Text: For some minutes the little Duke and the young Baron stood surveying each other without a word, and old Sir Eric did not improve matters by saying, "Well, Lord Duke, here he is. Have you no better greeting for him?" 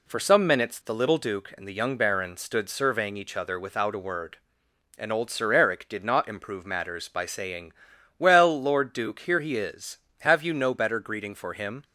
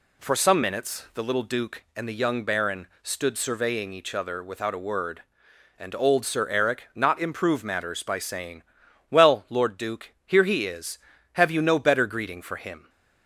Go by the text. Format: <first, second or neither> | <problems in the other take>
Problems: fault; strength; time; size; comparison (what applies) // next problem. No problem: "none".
first | pauses between "Baron" and "stood"; slight; at 2.8 s; 0.16 s long // skips "did"; at 6.9 s